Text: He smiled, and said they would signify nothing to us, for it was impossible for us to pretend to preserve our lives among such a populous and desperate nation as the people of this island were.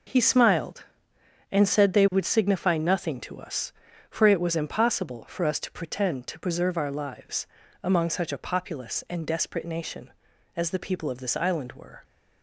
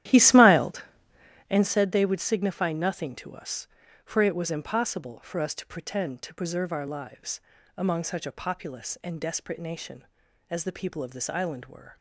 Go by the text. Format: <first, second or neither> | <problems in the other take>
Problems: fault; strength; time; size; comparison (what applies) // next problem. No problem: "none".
first | starts louder than the rest; strong; until 1.7 s; 12.5 dB // pauses between "lives" and "among"; slight; at 7.4 s; 0.34 s long; slight in the first